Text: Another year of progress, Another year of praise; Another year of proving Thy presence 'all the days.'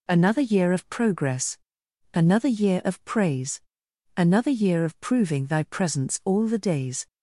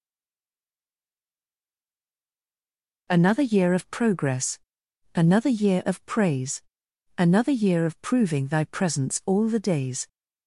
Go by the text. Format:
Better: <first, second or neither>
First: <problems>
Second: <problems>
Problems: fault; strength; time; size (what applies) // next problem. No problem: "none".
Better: first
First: none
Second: stays silent before the first word; strong; until 3.0 s; 3.0 s long